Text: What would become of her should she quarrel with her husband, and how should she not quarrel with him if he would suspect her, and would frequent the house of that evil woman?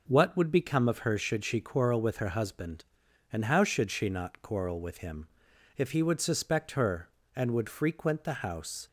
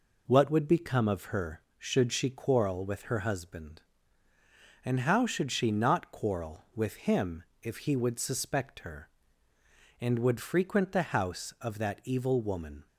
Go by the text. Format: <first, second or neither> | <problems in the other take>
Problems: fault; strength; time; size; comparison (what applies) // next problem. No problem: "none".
second | pauses between "him" and "if"; noticeable; at 5.2 s; 0.50 s long; slight in the second // stops before "of that evil woman"; at 8.8 s